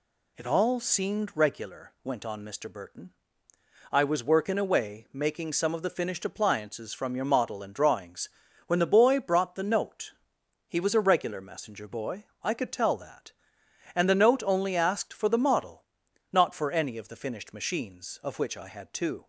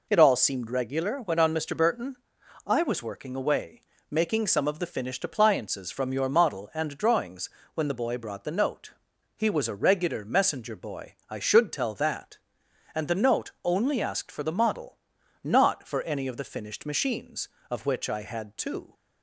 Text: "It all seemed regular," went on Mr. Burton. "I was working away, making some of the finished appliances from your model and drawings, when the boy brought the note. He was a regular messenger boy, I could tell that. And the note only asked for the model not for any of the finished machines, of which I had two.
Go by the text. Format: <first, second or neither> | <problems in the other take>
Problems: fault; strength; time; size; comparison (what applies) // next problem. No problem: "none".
first | says "should" for "could"; at 11.3 s // pauses between "model" and "not"; noticeable; at 14.9 s; 0.48 s long; noticeable in the first